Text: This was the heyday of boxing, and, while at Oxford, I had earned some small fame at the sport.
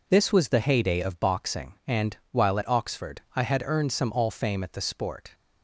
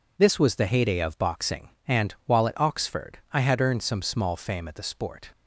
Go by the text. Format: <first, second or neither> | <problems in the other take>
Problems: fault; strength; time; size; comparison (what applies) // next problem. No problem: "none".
second | says "all" for "small"; at 4.1 s